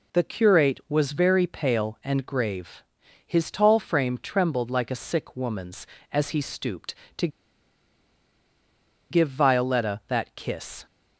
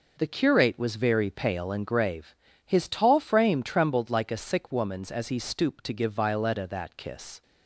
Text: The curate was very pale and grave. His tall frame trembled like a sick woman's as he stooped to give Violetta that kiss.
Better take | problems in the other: second | pauses between "to" and "give"; strong; at 7.2 s; 1.8 s long

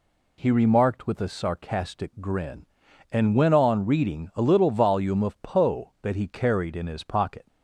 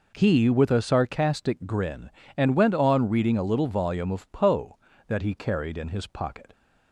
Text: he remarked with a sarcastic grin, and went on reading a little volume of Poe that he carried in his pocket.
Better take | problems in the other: first | skips "remarked"; at 0.4 s

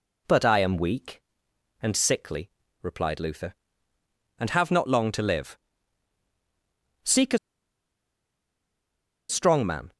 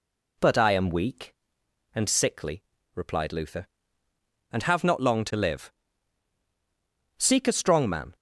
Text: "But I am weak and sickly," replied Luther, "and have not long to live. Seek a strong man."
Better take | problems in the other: second | pauses between "a" and "strong"; strong; at 7.3 s; 1.9 s long

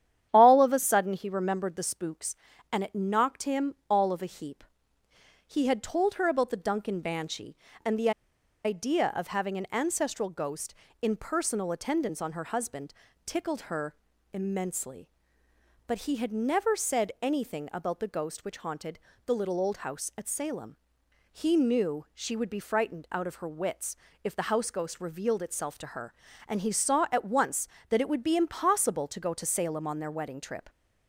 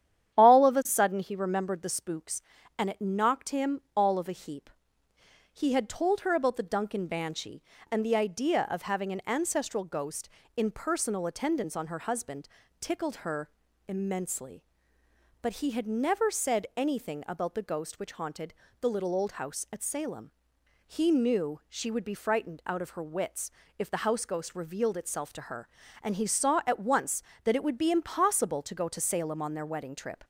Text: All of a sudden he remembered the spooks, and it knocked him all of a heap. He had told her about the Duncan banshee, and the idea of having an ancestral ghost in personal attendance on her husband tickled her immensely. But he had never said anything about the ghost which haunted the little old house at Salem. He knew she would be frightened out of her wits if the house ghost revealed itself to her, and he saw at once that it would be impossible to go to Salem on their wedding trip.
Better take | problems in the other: second | starts louder than the rest; strong; until 1.3 s; 10 dB; strong in the second // pauses between "him" and "all"; slight; at 3.7 s; 0.16 s long; slight in the second // pauses between "the" and "idea"; noticeable; at 8.1 s; 0.53 s long // pauses between "husband" and "tickled"; slight; at 12.9 s; 0.32 s long; slight in the second // pauses between "her" and "immensely"; at 13.9 s; 0.38 s long; also in the second // pauses between "haunted" and "the"; slight; at 18.9 s; 0.28 s long; slight in the second // pauses between "wits" and "if"; slight; at 23.9 s; 0.30 s long; slight in the second

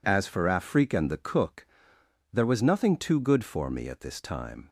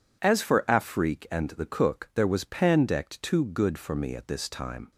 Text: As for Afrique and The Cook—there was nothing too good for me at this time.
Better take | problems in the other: first | says "pandect" for "nothing"; at 2.4 s

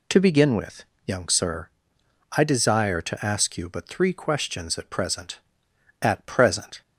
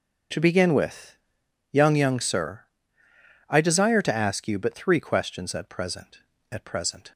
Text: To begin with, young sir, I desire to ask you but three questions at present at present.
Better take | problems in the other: first | starts louder than the rest; until 1.8 s; 6.5 dB // says "young" twice; at 1.9 s

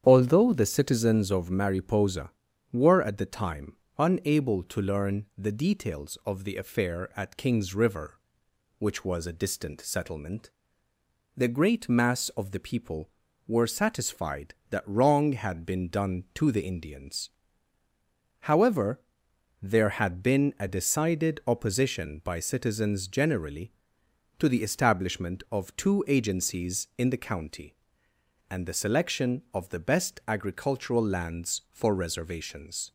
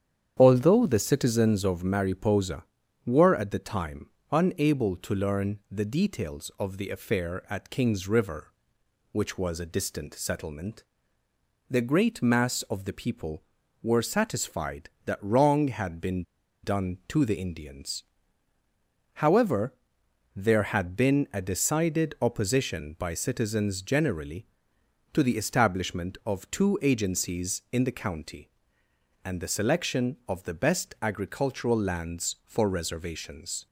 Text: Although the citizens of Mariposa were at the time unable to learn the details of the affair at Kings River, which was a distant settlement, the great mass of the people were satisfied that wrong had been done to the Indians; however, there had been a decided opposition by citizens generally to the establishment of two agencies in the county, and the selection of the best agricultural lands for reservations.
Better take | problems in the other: first | starts louder than the rest; strong; until 1.4 s; 9 dB; strong in the first // pauses between "time" and "unable"; slight; at 4.0 s; 0.20 s long; slight in the first // pauses between "been" and "done"; at 16.2 s; 0.41 s long

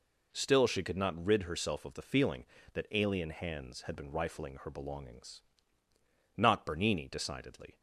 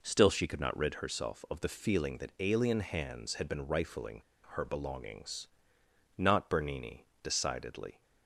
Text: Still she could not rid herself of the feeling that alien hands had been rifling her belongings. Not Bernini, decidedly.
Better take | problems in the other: first | pauses between "rifling" and "her"; slight; at 4.2 s; 0.27 s long

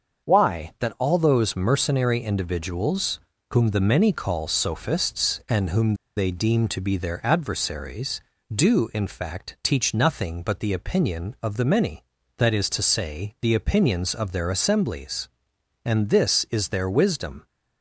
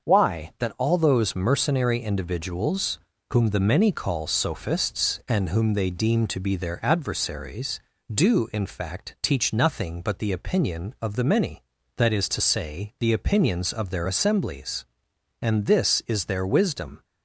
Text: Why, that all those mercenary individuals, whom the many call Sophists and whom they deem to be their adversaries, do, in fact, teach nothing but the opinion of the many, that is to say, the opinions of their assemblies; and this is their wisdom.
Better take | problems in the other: second | starts louder than the rest; until 1.3 s; 6.5 dB; also in the second // pauses between "whom" and "they"; slight; at 5.9 s; 0.22 s long

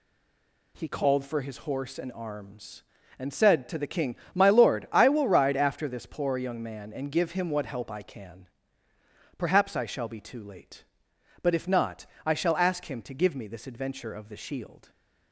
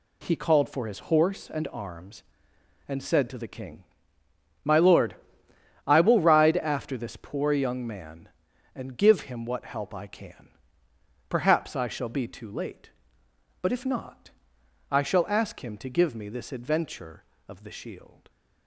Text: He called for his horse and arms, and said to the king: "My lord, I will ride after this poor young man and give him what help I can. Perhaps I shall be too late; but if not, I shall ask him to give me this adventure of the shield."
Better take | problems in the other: second | stays silent before the first word; slight; until 0.7 s; 0.7 s long

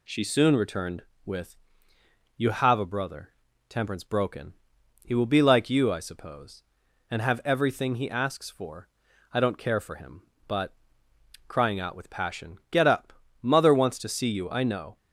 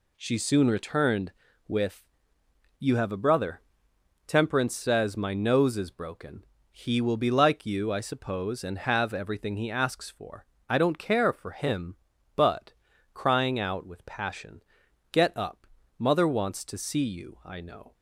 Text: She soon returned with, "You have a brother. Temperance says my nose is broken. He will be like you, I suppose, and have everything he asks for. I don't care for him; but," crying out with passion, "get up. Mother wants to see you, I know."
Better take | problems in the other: second | skips "says my nose is"; at 4.0 s

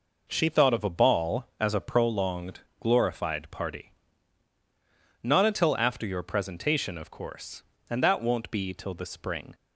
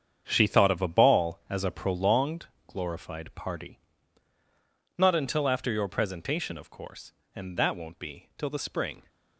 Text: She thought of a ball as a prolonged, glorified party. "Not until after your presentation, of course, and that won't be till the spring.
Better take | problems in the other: first | gets quieter; strong; throughout; 11 dB

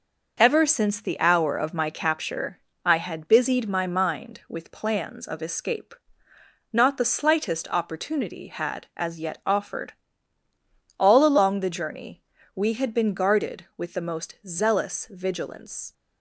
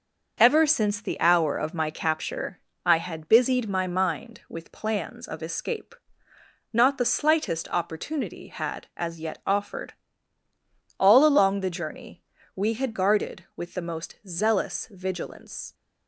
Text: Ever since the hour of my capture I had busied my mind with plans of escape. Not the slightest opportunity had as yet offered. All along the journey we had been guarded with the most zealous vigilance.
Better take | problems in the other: first | pauses between "capture" and "I"; slight; at 2.6 s; 0.24 s long; slight in the first // pauses between "journey" and "we"; slight; at 12.2 s; 0.32 s long; slight in the first // skips "been"; at 12.9 s

